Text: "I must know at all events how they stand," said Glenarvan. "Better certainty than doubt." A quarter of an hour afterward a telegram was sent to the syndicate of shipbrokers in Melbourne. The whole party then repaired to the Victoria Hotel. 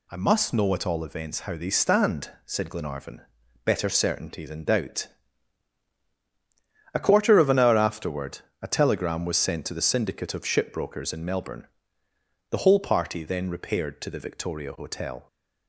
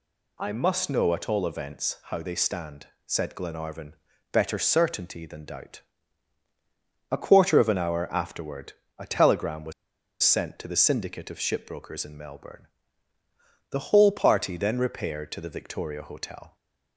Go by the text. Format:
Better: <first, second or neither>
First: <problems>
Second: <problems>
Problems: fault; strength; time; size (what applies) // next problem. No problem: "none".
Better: first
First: pauses between "afterward" and "a"; slight; at 8.3 s; 0.22 s long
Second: pauses between "afterward" and "a"; slight; at 8.7 s; 0.26 s long // pauses between "was" and "sent"; noticeable; at 9.7 s; 0.50 s long